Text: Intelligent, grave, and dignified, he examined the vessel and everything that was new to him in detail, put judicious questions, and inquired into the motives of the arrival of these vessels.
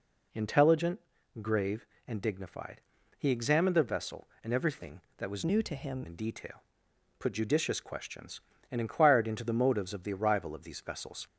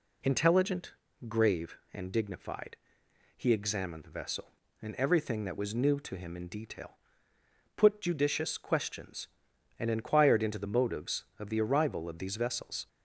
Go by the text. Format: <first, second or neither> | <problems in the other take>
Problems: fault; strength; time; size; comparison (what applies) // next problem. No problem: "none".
second | changes voice from "new" to "him"; from 5.4 to 6.0 s; 0.6 s long